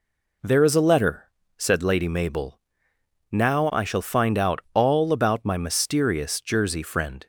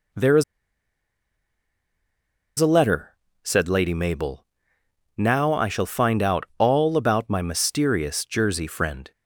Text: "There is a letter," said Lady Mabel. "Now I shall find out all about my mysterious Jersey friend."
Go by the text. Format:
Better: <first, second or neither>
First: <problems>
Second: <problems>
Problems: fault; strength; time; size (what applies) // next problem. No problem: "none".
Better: first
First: none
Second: pauses between "is" and "a"; strong; at 0.4 s; 2.1 s long